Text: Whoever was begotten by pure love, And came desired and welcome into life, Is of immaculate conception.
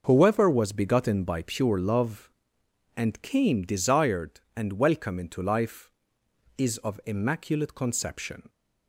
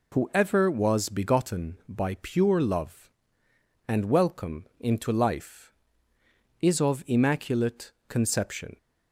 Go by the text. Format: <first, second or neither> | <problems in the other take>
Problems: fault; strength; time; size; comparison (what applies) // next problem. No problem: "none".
first | skips "came desired and"; at 4.0 s // pauses between "immaculate" and "conception"; slight; at 7.9 s; 0.16 s long